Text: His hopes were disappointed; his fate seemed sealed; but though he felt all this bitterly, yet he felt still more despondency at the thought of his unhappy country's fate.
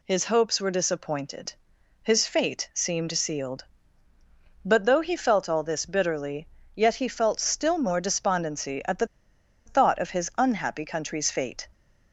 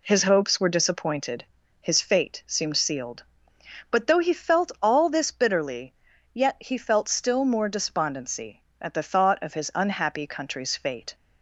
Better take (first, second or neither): second